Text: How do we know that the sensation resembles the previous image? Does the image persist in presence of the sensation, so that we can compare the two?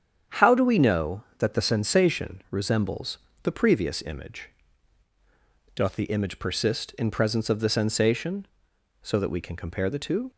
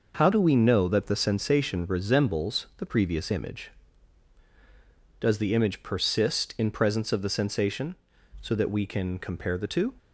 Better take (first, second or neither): second